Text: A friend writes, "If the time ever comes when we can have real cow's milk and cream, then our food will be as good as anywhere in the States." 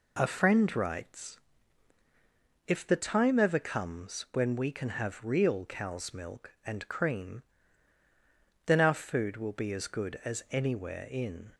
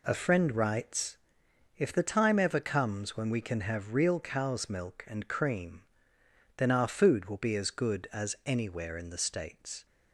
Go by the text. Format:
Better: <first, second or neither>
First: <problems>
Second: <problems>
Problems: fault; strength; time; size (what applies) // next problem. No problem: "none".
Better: second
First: stops before "the States"; at 11.5 s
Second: none